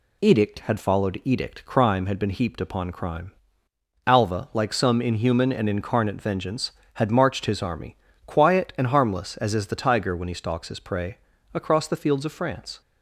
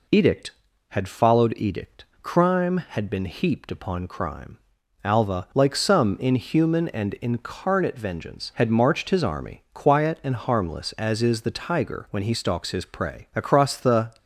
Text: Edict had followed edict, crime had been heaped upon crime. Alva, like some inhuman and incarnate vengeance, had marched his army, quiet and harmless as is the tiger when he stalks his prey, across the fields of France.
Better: first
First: none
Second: stops before "fields of France"; at 14.1 s

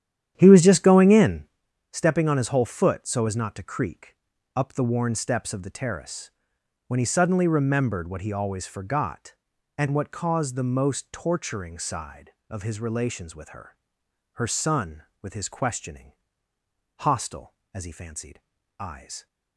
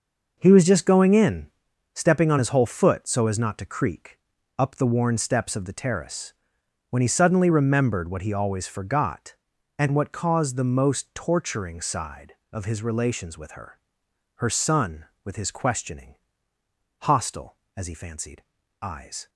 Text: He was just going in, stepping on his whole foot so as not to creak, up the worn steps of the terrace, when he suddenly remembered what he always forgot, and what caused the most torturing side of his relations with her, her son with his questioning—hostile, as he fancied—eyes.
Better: second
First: starts louder than the rest; strong; until 1.4 s; 10.5 dB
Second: none

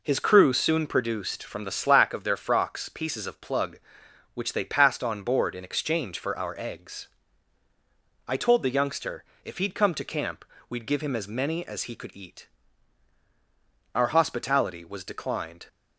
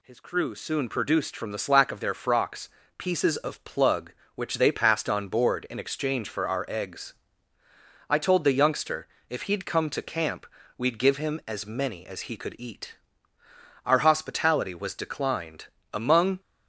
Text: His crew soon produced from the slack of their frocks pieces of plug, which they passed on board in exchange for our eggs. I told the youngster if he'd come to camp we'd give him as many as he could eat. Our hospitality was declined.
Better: first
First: pauses between "youngster" and "if"; slight; at 9.2 s; 0.22 s long // pauses between "camp" and "we'd"; slight; at 10.4 s; 0.24 s long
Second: pauses between "frocks" and "pieces"; slight; at 2.6 s; 0.30 s long // pauses between "youngster" and "if"; slight; at 9.0 s; 0.24 s long // pauses between "camp" and "we'd"; slight; at 10.4 s; 0.30 s long // goes on to say "Among"; slight; from 15.9 s on; 0.46 s long

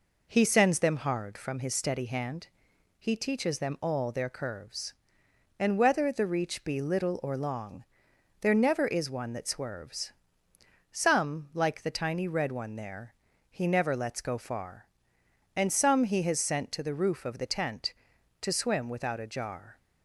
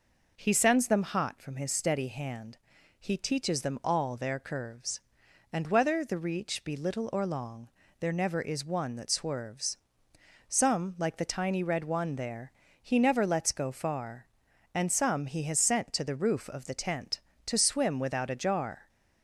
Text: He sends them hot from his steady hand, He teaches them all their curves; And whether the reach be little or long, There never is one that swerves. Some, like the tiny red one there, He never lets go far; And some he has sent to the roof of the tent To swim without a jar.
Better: second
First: says "hard" for "hot"; at 0.9 s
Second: none

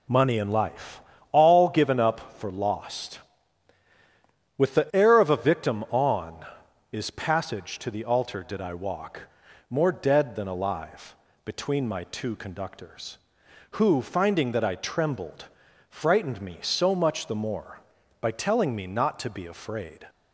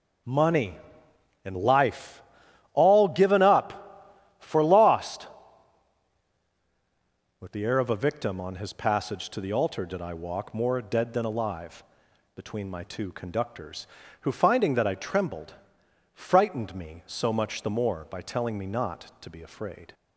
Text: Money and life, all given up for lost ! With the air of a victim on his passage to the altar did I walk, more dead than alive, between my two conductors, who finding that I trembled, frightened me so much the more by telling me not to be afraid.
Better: second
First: says "is" for "his"; at 6.9 s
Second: none

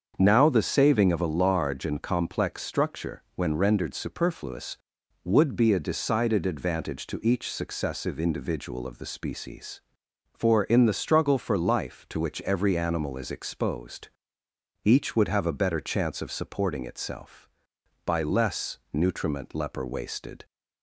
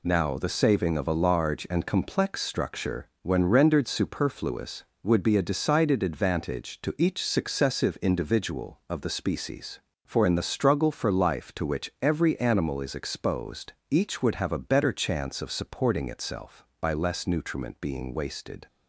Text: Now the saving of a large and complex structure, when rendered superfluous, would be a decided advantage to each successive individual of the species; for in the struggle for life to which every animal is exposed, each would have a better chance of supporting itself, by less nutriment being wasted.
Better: second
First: starts louder than the rest; until 1.1 s; 7 dB // says "leper" for "being"; at 19.5 s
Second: none

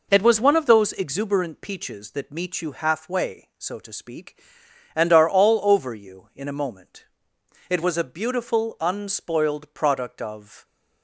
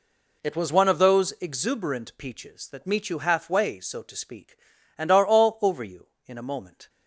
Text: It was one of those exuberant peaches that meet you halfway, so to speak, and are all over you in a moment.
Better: second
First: goes on to say "It was a beautiful unspoiled product of"; strong; from 7.6 s on; 2.9 s long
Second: none

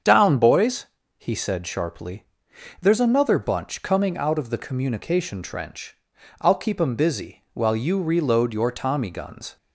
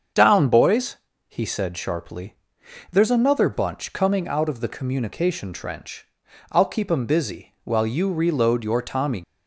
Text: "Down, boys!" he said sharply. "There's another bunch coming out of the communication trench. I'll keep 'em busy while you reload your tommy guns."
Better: first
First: starts louder than the rest; strong; until 1.3 s; 7.5 dB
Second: starts louder than the rest; until 1.4 s; 7 dB // stops before "guns"; at 9.2 s

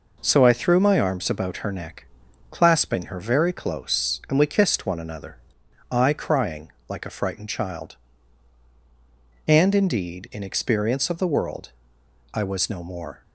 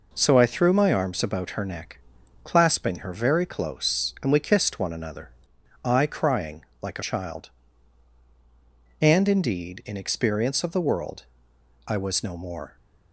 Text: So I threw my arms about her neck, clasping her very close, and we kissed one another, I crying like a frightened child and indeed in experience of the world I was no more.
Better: first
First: pauses between "crying" and "like"; slight; at 6.7 s; 0.18 s long // pauses between "world" and "I"; noticeable; at 11.7 s; 0.62 s long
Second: pauses between "crying" and "like"; slight; at 6.6 s; 0.18 s long // skips "frightened"; at 7.0 s // pauses between "world" and "I"; noticeable; at 11.2 s; 0.62 s long

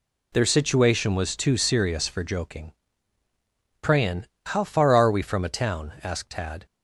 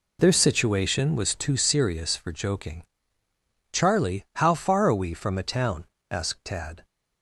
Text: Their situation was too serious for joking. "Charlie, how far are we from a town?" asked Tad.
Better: second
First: says "Prayin" for "Charlie"; at 3.8 s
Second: none

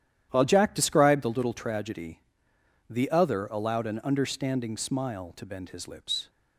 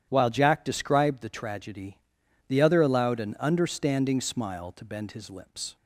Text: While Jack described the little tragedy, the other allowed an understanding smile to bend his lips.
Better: first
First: starts louder than the rest; strong; until 1.3 s; 11 dB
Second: starts louder than the rest; strong; until 1.1 s; 10 dB // skips "little"; at 1.2 s

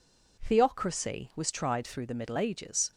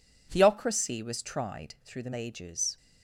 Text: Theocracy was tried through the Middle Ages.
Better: first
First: none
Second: skips "Middle"; at 2.1 s

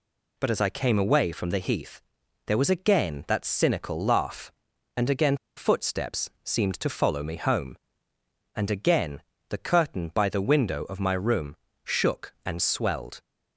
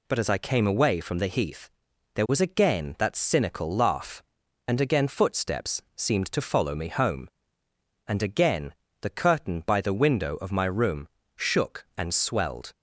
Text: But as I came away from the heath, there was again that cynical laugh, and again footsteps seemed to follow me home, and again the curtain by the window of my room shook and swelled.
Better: second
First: pauses between "again" and "footsteps"; slight; at 5.3 s; 0.19 s long // pauses between "again" and "the"; slight; at 9.1 s; 0.30 s long // pauses between "room" and "shook"; slight; at 11.5 s; 0.28 s long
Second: pauses between "again" and "the"; slight; at 8.7 s; 0.30 s long // pauses between "room" and "shook"; slight; at 11.0 s; 0.28 s long

